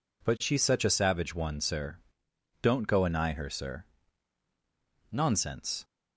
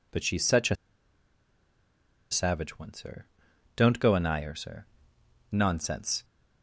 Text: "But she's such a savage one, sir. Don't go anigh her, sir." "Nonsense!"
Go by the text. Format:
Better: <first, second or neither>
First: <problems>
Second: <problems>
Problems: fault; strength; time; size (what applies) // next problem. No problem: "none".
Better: first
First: none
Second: pauses between "a" and "savage"; strong; at 0.7 s; 1.5 s long